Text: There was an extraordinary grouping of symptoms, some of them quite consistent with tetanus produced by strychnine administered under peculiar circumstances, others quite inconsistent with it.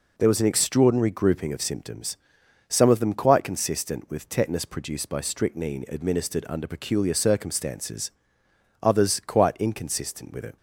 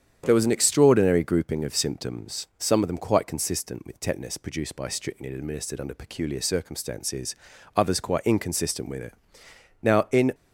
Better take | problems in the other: first | starts louder than the rest; strong; until 1.2 s; 8.5 dB // goes on to say "Now in"; from 9.8 s on; 0.50 s long

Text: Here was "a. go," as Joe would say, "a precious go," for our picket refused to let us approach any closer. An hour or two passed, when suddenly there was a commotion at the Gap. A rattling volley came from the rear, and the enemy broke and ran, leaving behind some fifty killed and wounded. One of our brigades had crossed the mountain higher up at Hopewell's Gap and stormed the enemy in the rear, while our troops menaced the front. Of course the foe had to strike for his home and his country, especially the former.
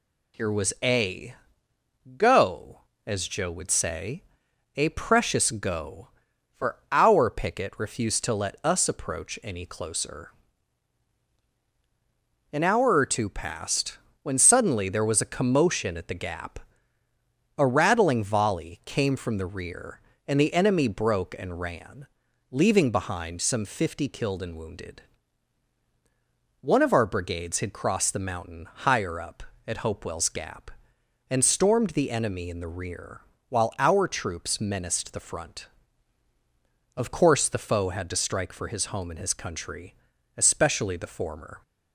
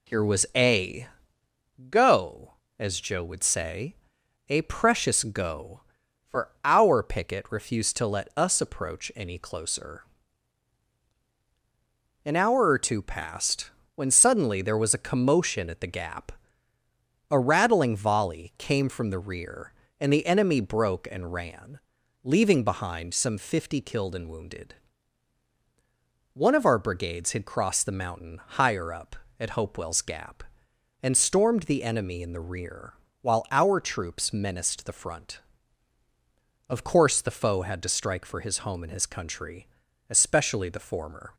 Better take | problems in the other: first | starts louder than the rest; slight; until 1.5 s; 2 dB

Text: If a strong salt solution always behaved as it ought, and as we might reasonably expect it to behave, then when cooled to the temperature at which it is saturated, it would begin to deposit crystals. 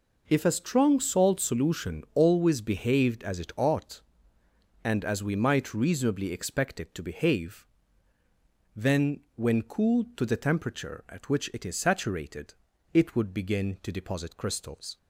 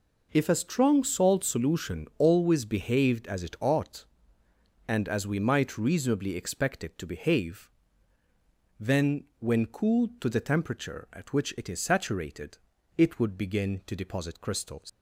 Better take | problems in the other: first | leaves "crystals" unfinished; at 14.8 s; 110 ms

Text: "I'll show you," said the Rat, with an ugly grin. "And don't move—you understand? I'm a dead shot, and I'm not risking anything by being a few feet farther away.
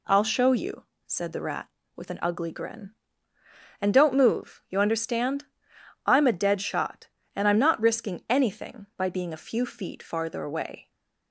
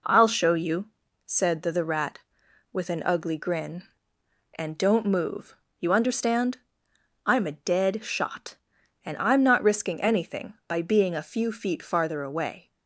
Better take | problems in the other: first | says "the" twice; at 1.7 s

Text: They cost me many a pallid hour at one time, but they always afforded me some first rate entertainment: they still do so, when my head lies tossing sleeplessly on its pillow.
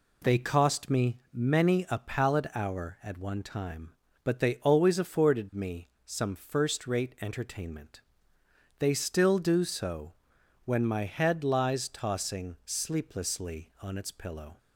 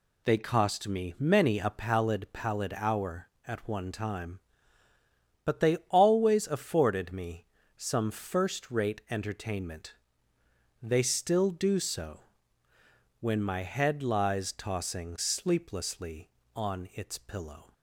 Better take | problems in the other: first | says "pallid" twice; at 2.3 s // pauses between "me" and "some"; slight; at 7.4 s; 0.32 s long; slight in the first

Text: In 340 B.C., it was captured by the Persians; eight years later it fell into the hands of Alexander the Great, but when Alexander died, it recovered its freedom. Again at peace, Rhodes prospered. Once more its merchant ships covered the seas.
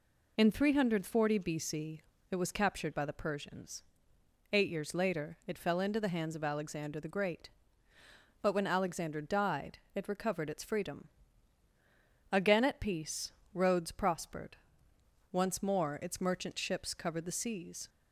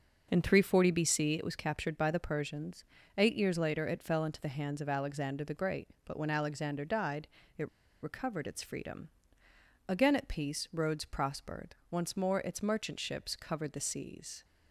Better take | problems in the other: first | pauses between "it" and "recovered"; slight; at 7.6 s; 0.32 s long

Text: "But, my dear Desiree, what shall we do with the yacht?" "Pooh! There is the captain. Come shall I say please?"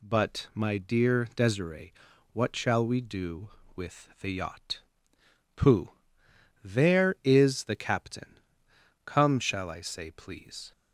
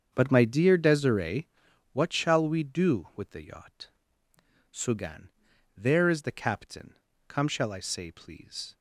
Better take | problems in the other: first | starts louder than the rest; strong; until 1.1 s; 7.5 dB // says "Sugan" for "Pooh"; at 4.7 s

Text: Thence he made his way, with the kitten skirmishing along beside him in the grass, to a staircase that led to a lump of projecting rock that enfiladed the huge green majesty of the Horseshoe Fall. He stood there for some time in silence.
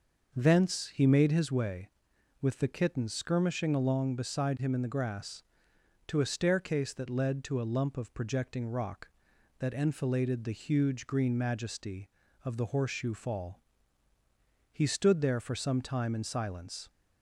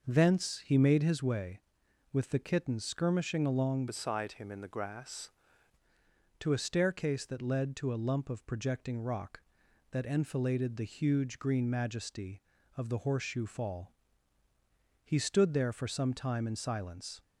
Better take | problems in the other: first | starts louder than the rest; noticeable; until 1.1 s; 6 dB; noticeable in the first // changes voice from "beside" to "grass"; from 3.8 to 5.3 s; 1.5 s long

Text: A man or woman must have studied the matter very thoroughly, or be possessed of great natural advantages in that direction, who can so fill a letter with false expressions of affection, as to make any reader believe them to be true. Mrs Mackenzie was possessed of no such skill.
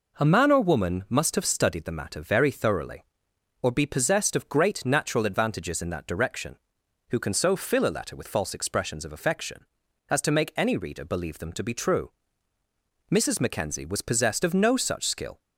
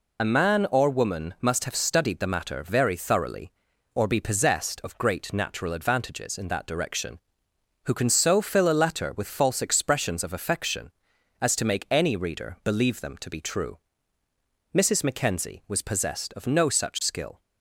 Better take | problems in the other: first | loses the start of "A"; at 0.1 s; 30 ms

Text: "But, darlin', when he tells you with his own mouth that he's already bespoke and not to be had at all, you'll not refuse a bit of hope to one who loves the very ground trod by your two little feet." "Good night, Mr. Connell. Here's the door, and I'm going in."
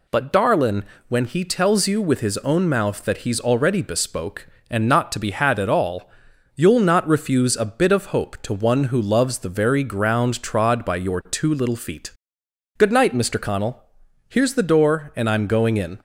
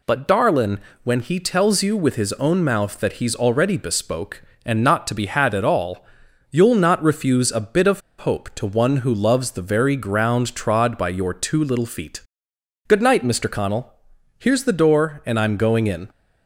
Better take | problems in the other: first | pauses between "of" and "hope"; slight; at 8.0 s; 0.19 s long

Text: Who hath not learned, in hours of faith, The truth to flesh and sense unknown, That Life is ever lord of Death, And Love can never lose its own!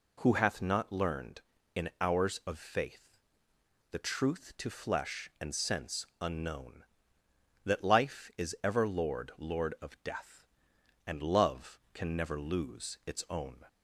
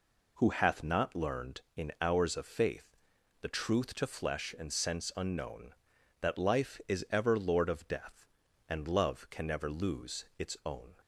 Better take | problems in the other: second | says "lord" twice; at 9.3 s

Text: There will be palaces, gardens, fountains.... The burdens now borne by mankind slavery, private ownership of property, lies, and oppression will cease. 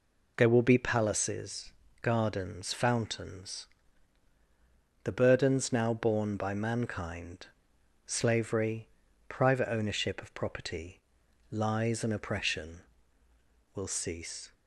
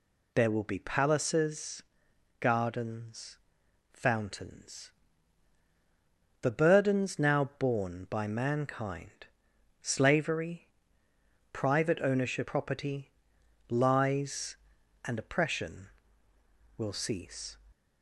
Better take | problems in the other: first | pauses between "mankind" and "slavery"; noticeable; at 9.2 s; 0.56 s long; noticeable in the first // skips "of"; at 12.4 s

